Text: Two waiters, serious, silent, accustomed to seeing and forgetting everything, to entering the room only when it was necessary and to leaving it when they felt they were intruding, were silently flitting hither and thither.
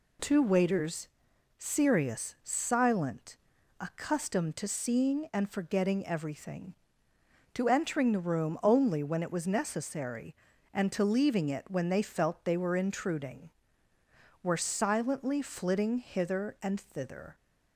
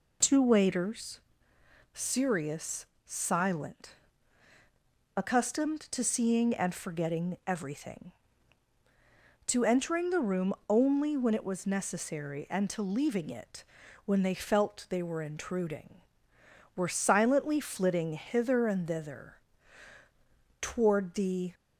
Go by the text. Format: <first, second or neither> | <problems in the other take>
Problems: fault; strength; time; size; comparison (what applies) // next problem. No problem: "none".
first | pauses between "room" and "only"; slight; at 10.5 s; 0.16 s long // pauses between "it" and "when"; at 13.6 s; 0.40 s long // goes on to say "Toward the"; noticeable; from 20.6 s on; 0.92 s long